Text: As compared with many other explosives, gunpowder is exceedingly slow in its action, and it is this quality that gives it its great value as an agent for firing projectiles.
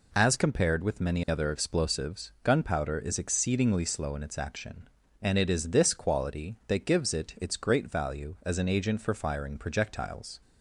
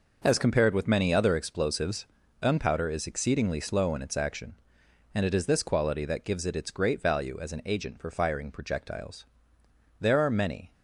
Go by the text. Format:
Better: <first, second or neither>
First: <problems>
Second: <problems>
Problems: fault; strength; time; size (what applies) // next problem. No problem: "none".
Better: first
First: none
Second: goes on to say "There are many"; noticeable; from 9.9 s on; 0.72 s long